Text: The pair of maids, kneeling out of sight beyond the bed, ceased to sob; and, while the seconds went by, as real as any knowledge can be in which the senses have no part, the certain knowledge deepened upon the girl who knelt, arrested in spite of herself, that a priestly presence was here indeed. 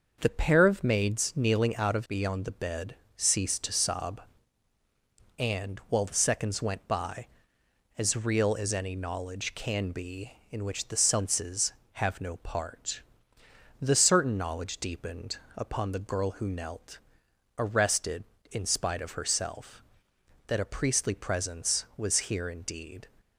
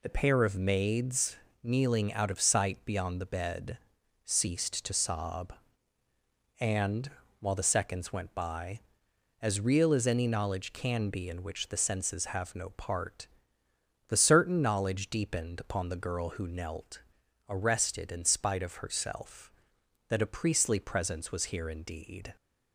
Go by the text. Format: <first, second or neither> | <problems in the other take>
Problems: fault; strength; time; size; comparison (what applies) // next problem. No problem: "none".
second | starts louder than the rest; noticeable; until 1.2 s; 6 dB // skips "sight"; at 2.0 s // pauses between "deepened" and "upon"; slight; at 15.3 s; 0.18 s long